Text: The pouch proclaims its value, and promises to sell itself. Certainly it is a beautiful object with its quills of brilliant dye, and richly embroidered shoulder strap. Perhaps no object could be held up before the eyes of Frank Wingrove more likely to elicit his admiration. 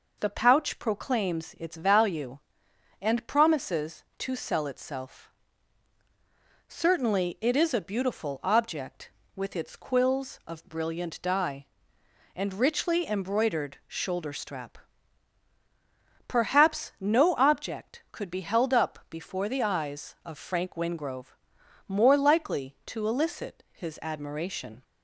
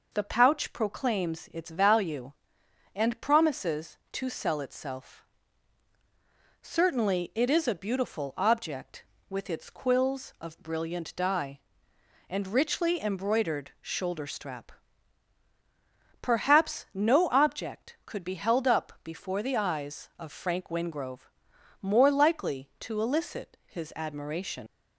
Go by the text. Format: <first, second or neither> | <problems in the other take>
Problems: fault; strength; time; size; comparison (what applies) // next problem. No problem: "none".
first | pauses between "Wingrove" and "more"; noticeable; at 21.3 s; 0.50 s long; noticeable in the first // leaves "admiration" unfinished; at 24.6 s; 100 ms